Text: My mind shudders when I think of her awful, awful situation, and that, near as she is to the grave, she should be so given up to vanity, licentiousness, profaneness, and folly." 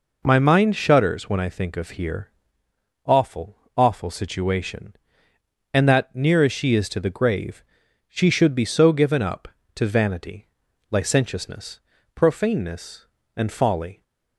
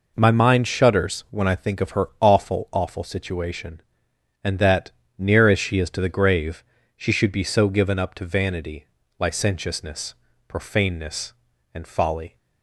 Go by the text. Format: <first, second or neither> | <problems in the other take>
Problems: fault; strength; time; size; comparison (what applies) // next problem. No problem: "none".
second | says "here" for "her"; at 1.9 s